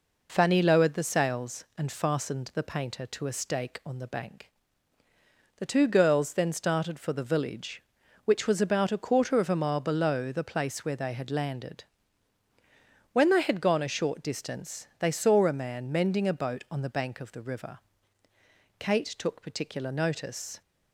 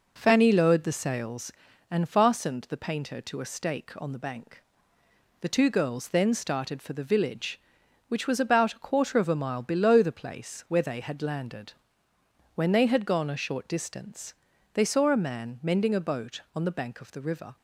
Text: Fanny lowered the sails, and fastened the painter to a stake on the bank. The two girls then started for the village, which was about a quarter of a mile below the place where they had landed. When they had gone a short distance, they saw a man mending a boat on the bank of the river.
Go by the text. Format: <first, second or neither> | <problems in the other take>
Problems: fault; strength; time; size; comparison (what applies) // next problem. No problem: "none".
second | goes on to say "Kate took particular notice"; strong; from 18.7 s on; 1.8 s long